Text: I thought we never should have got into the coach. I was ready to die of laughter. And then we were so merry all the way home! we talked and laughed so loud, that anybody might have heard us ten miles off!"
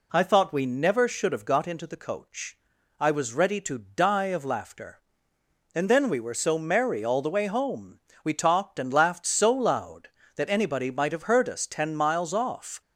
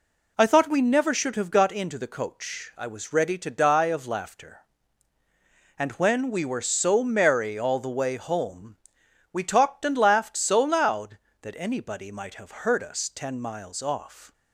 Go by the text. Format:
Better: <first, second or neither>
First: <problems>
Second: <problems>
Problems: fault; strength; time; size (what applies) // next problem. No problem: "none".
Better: first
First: none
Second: says "when" for "then"; at 5.9 s